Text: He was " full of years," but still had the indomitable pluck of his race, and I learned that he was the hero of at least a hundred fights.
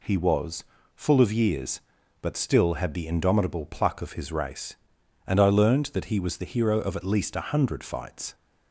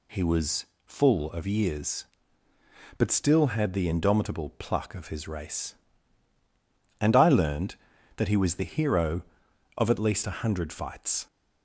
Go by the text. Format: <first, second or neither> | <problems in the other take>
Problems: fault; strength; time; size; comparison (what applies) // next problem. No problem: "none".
neither | none